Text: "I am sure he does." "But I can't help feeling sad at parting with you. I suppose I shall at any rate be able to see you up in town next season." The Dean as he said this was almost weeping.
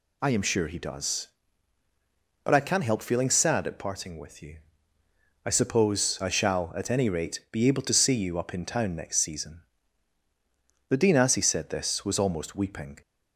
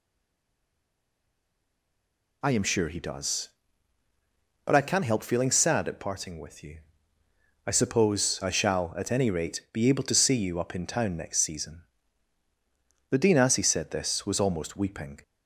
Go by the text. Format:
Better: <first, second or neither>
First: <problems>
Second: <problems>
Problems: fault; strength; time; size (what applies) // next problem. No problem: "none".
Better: first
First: none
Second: stays silent before the first word; until 2.4 s; 2.4 s long